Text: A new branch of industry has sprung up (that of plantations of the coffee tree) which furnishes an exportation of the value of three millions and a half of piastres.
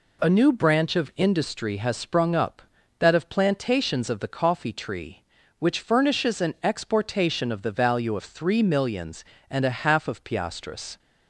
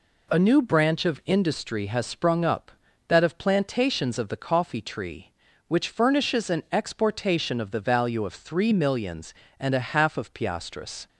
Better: neither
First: none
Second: none

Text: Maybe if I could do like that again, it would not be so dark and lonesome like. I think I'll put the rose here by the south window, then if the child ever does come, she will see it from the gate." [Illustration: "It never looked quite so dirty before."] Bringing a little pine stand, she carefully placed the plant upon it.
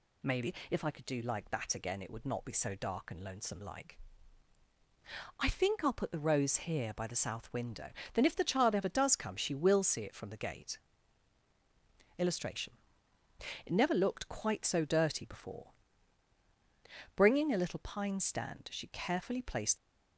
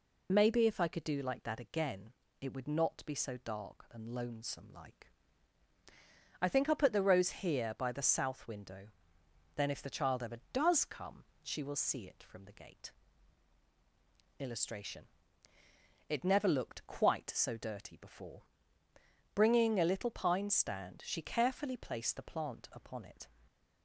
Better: second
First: pauses between "Maybe" and "if"; slight; at 0.5 s; 0.16 s long // stops before "the plant upon it"; at 19.7 s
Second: none

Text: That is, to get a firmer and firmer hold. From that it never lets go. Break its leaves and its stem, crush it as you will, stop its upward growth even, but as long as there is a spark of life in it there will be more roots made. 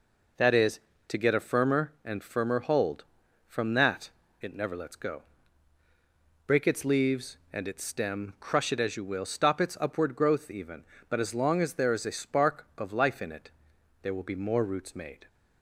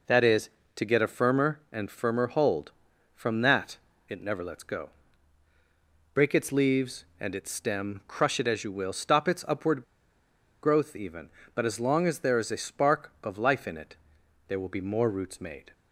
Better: first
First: pauses between "that" and "it"; slight; at 4.0 s; 0.32 s long // pauses between "it" and "there"; noticeable; at 13.5 s; 0.52 s long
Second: pauses between "that" and "it"; slight; at 3.7 s; 0.32 s long // pauses between "upward" and "growth"; noticeable; at 9.8 s; 0.80 s long // pauses between "it" and "there"; noticeable; at 13.9 s; 0.52 s long

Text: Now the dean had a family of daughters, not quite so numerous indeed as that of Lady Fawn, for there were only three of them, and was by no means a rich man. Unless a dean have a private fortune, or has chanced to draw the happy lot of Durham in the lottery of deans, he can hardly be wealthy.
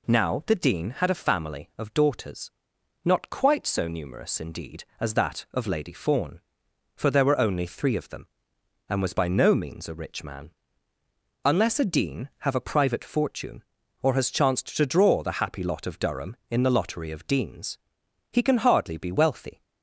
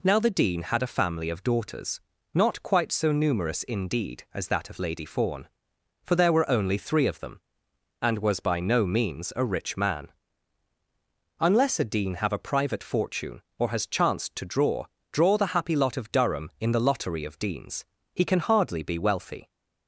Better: first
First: none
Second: says "draw" twice; at 15.1 s

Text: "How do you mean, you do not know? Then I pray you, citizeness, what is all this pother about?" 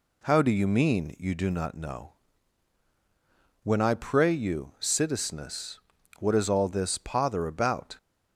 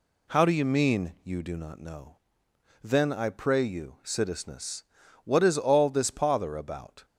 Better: second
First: says "When" for "Then"; at 3.6 s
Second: none

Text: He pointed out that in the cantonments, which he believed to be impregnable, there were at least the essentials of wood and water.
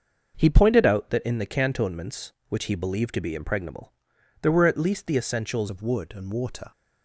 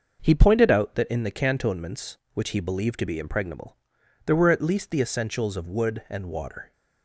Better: second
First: changes voice at "of"; from 5.6 s on; 1.1 s long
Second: none

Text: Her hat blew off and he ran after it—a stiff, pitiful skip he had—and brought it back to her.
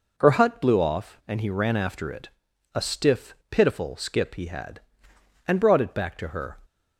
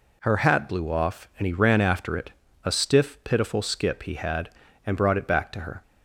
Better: second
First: says "hut" for "hat"; at 0.3 s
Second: none

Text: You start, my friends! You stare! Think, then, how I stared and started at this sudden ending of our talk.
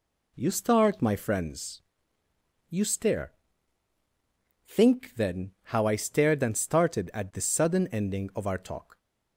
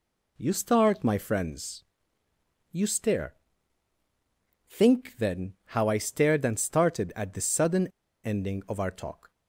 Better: first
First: none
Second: pauses between "sudden" and "ending"; slight; at 7.8 s; 0.35 s long

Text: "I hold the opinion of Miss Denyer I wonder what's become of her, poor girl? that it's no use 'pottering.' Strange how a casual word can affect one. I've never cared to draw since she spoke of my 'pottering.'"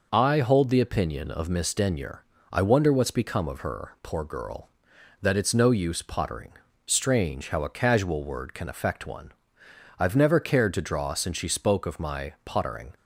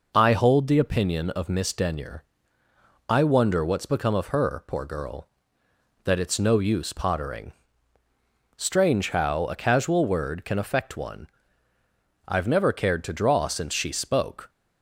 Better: first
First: pauses between "Denyer" and "I"; slight; at 2.2 s; 0.28 s long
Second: pauses between "Denyer" and "I"; noticeable; at 2.2 s; 0.84 s long // stops before "of my pottering"; at 14.4 s

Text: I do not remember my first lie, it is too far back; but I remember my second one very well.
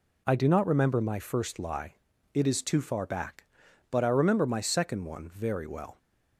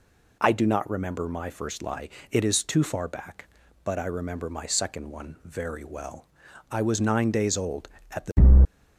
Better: first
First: none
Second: goes on to say "I was nine days old at the"; strong; from 6.7 s on; 1.7 s long

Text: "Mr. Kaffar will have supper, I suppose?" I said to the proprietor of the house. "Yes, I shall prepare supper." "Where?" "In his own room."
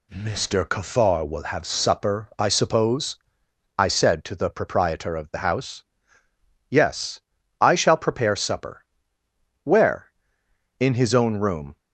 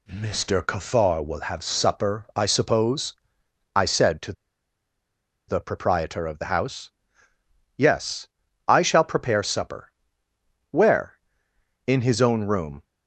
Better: first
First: none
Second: pauses between "to" and "the"; at 4.3 s; 1.1 s long

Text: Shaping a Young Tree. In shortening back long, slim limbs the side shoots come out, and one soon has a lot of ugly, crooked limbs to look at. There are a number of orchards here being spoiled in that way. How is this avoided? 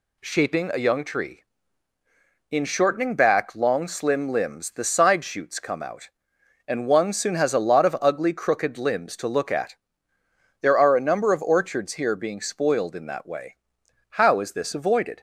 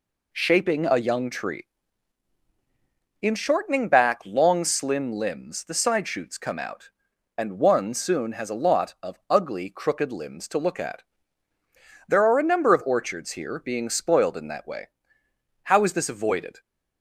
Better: neither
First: none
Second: none

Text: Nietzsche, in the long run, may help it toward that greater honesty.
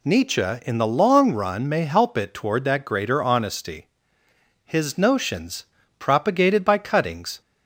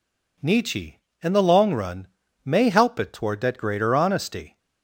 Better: second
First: goes on to say "His notions propagated by cuttings"; strong; from 4.6 s on; 2.7 s long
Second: none

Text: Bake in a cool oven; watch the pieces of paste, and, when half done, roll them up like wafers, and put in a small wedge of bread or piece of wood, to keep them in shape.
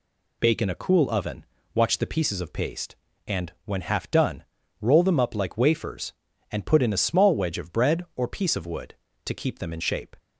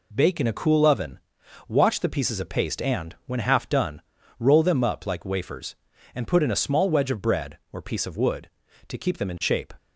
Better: neither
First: none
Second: none

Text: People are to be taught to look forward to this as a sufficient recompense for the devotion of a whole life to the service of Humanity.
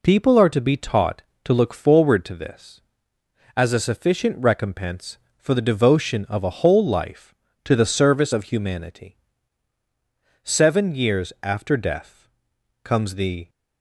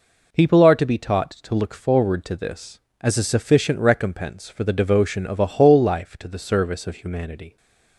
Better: second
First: goes on to say "Seven years after death comes the"; strong; from 10.4 s on; 3.0 s long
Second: none

